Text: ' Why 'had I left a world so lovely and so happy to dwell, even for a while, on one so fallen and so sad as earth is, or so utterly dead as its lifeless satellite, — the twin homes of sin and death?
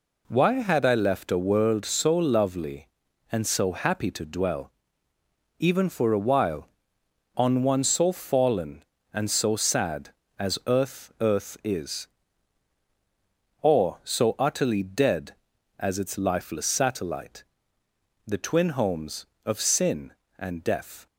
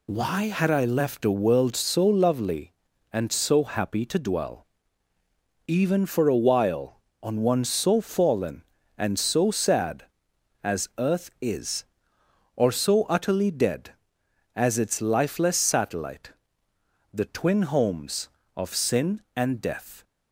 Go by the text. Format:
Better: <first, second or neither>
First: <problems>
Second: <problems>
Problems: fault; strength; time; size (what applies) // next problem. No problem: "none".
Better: second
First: says "earth" twice; at 11.1 s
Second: none